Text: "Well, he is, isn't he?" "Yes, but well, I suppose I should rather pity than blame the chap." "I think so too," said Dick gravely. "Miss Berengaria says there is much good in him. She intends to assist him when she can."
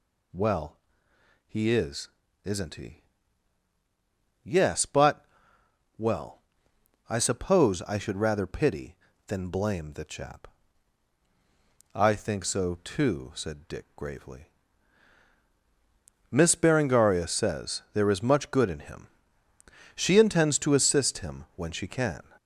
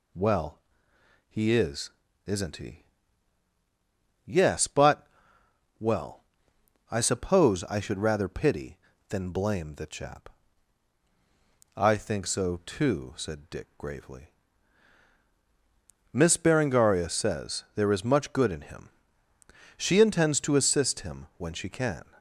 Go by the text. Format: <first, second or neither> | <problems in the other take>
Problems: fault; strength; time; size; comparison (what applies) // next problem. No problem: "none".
second | gets louder; noticeable; throughout; 5.5 dB // pauses between "but" and "well"; noticeable; at 5.2 s; 0.74 s long; noticeable in the second